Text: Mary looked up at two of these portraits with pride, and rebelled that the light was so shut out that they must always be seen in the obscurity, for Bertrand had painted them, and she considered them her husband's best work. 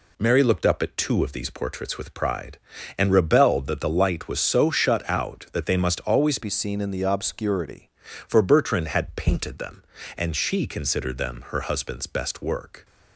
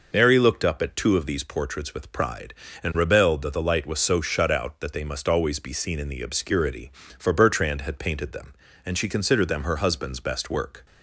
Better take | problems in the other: second | changes voice from "be" to "obscurity"; from 6.4 to 7.8 s; 1.4 s long

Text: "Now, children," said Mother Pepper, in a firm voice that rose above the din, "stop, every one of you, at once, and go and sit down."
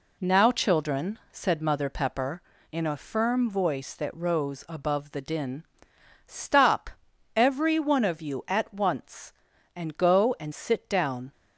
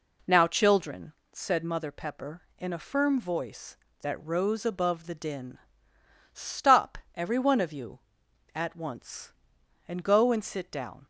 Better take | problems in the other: neither | none

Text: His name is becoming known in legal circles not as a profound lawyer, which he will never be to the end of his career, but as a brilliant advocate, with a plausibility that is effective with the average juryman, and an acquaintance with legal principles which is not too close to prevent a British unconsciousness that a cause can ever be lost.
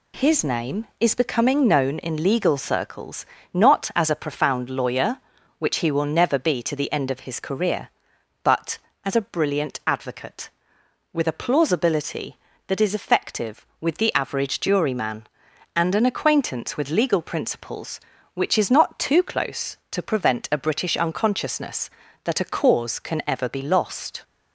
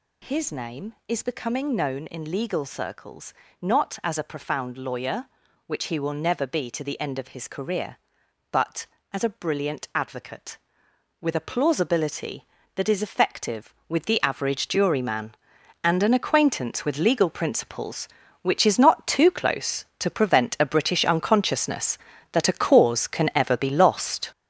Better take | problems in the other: first | gets louder; strong; throughout; 8 dB // pauses between "circles" and "not"; slight; at 3.3 s; 0.28 s long; slight in the first

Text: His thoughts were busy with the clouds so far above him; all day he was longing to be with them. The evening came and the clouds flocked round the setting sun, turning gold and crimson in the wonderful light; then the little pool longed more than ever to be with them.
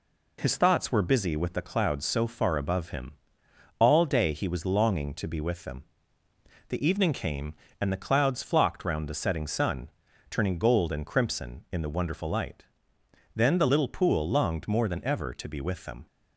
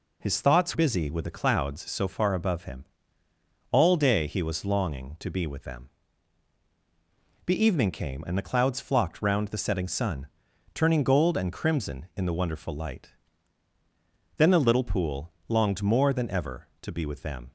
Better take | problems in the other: first | skips "were"; at 0.7 s // pauses between "pool" and "longed"; slight; at 15.3 s; 0.16 s long

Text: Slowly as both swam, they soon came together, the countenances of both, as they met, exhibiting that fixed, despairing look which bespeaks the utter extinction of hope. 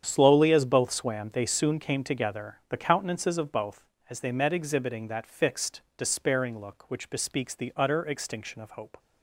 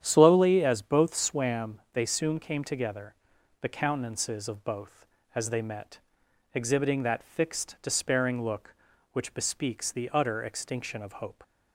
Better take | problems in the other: neither | starts louder than the rest; strong; the same in both

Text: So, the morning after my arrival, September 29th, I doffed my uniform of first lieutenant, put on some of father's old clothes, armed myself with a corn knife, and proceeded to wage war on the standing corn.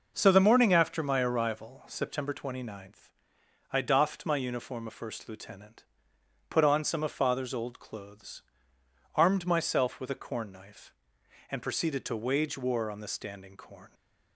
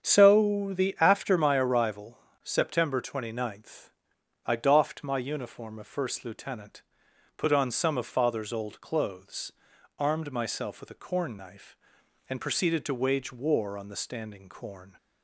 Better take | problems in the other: first | starts louder than the rest; strong; until 1.0 s; 7.5 dB // skips "morning"; at 0.9 s

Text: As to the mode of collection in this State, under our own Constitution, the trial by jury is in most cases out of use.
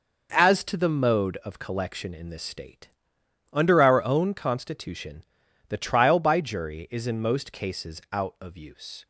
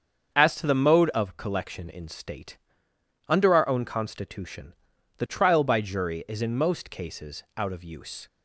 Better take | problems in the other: first | starts louder than the rest; until 1.3 s; 7 dB // skips "this"; at 2.0 s

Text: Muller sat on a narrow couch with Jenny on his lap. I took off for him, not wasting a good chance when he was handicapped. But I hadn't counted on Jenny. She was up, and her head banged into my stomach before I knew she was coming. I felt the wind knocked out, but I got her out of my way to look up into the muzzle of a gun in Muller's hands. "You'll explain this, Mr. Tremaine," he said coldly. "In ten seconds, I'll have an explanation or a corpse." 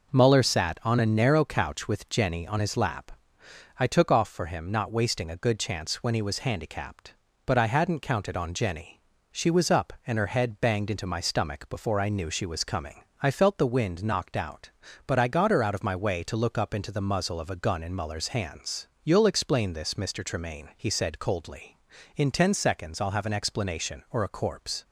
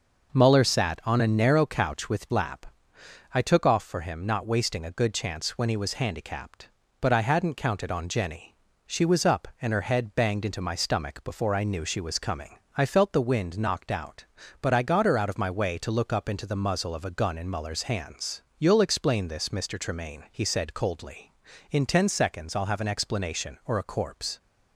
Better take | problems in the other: first | skips "Jenny on his"; at 2.3 s

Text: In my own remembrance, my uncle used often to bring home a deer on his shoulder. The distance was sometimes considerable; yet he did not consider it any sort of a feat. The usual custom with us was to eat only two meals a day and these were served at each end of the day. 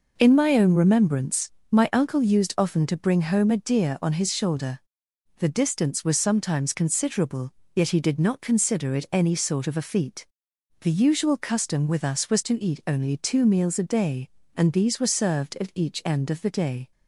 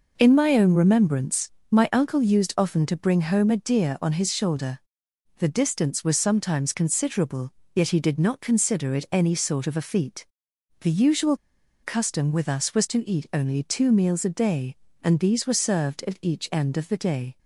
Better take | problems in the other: first | pauses between "usual" and "custom"; noticeable; at 11.3 s; 0.47 s long

